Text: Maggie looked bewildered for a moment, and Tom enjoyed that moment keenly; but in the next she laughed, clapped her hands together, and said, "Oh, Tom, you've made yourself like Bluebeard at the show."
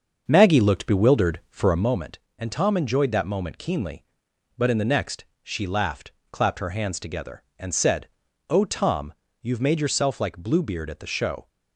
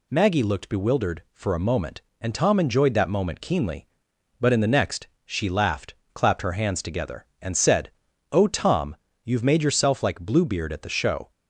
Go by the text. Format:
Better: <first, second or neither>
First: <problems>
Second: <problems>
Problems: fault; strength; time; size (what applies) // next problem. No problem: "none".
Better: second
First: starts louder than the rest; until 2.0 s; 6.5 dB // pauses between "next" and "she"; slight; at 5.2 s; 0.18 s long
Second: pauses between "next" and "she"; slight; at 5.0 s; 0.18 s long